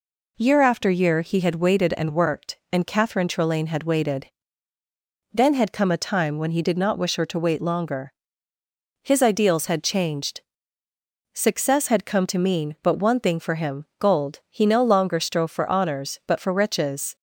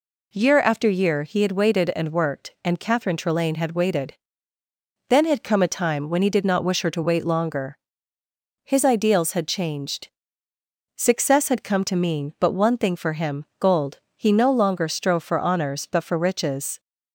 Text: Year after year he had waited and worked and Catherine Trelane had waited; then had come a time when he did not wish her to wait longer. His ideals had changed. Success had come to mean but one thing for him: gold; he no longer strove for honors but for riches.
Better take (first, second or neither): neither